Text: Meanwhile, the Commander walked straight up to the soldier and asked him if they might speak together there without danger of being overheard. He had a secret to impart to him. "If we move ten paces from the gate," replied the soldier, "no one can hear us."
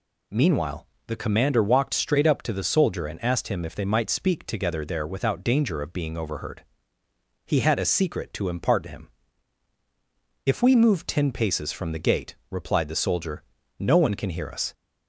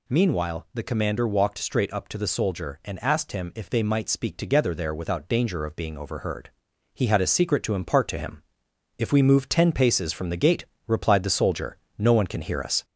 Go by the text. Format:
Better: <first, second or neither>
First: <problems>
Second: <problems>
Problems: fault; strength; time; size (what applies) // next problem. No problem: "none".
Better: first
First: none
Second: gets louder; slight; throughout; 3 dB